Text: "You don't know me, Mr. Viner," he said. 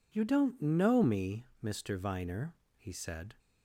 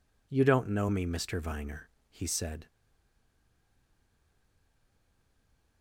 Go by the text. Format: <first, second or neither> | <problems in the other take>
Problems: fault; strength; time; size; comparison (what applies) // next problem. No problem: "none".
first | stays silent after the last word; strong; from 2.6 s on; 3.2 s long